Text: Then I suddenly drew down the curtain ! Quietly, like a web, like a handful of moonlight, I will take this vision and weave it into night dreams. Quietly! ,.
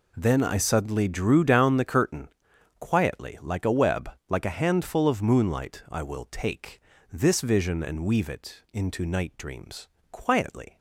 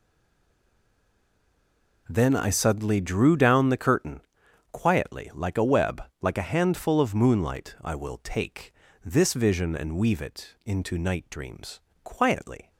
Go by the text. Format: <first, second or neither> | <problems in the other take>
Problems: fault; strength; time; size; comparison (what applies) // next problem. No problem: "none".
first | stays silent before the first word; noticeable; until 2.0 s; 2.0 s long // pauses between "take" and "this"; slight; at 8.7 s; 0.32 s long; slight in the first